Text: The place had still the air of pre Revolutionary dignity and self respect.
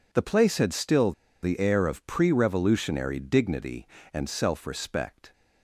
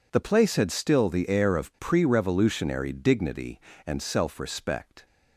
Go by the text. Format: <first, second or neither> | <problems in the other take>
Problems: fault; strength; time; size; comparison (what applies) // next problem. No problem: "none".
second | pauses between "still" and "the"; slight; at 1.1 s; 0.31 s long